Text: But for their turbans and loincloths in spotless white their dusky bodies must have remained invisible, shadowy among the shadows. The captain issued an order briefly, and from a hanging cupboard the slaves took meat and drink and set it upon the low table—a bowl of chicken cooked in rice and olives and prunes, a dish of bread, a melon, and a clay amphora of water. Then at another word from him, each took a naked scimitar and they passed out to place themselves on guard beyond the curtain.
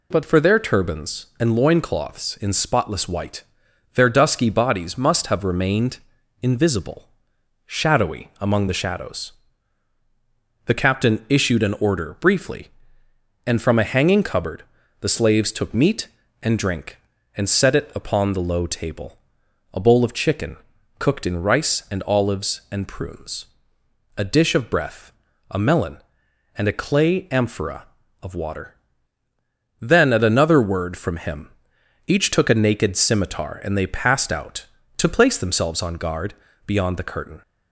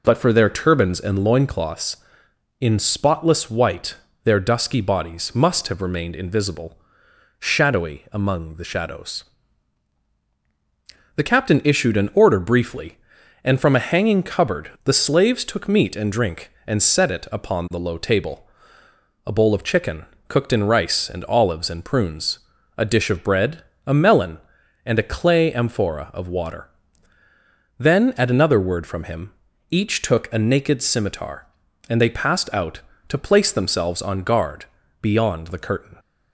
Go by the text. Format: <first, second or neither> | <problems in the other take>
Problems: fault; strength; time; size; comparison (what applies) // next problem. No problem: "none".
second | pauses between "white" and "their"; noticeable; at 3.4 s; 0.50 s long; slight in the second // pauses between "remained" and "invisible"; at 5.9 s; 0.44 s long // pauses between "cupboard" and "the"; at 14.6 s; 0.38 s long // pauses between "chicken" and "cooked"; at 20.5 s; 0.42 s long; slight in the second // says "breath" for "bread"; at 24.6 s // pauses between "guard" and "beyond"; slight; at 36.3 s; 0.32 s long; also in the second